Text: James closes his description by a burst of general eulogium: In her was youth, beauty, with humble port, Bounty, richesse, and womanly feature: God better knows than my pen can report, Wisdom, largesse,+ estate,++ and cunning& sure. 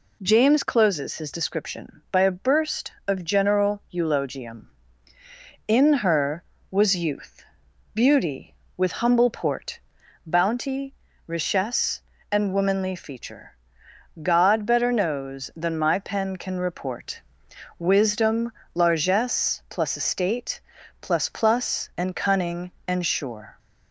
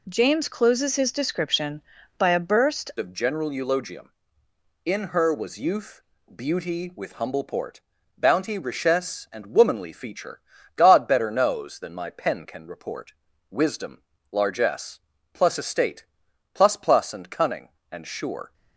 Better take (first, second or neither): first